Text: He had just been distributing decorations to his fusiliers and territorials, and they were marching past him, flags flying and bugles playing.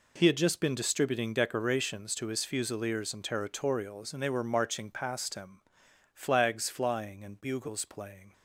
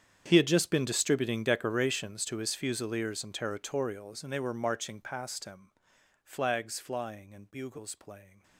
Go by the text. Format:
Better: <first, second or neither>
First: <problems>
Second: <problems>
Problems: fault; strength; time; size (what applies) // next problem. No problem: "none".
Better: first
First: none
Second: gets quieter; strong; throughout; 20.5 dB